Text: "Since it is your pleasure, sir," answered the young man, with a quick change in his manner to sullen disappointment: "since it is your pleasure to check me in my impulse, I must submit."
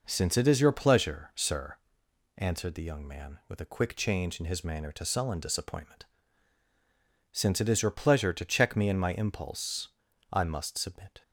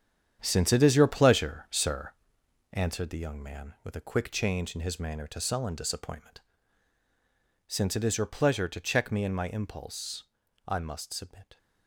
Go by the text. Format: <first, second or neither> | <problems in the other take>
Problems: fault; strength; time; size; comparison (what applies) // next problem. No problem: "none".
first | gets quieter; strong; throughout; 10 dB